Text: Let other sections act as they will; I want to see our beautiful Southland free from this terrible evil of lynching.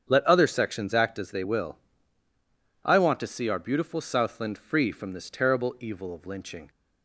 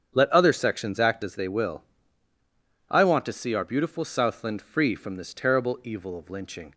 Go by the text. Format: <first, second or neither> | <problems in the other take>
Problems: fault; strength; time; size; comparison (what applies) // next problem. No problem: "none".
neither | starts louder than the rest; strong; the same in both